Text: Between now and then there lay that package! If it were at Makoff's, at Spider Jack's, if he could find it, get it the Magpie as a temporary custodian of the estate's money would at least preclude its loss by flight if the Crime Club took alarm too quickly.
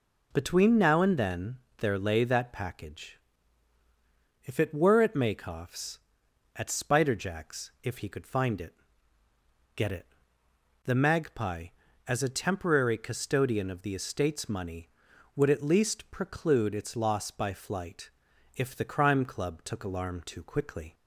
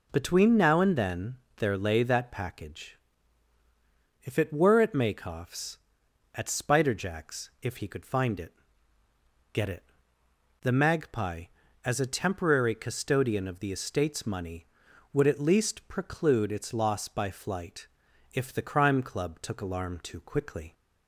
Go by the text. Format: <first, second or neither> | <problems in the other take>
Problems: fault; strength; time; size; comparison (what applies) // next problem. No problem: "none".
neither | pauses between "then" and "there"; slight; the same in both // pauses between "it" and "the"; noticeable; the same in both // pauses between "flight" and "if"; noticeable; the same in both